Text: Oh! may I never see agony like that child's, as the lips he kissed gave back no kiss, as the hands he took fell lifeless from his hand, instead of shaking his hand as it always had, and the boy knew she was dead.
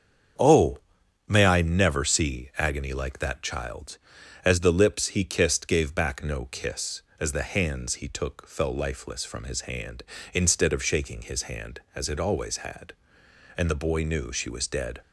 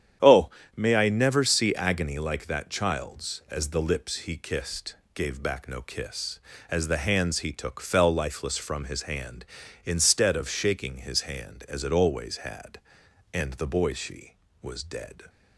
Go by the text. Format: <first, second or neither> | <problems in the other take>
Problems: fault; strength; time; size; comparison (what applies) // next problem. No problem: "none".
first | starts louder than the rest; strong; until 1.4 s; 9.5 dB; strong in the first // pauses between "kissed" and "gave"; slight; at 4.9 s; 0.18 s long // skips "knew"; at 13.9 s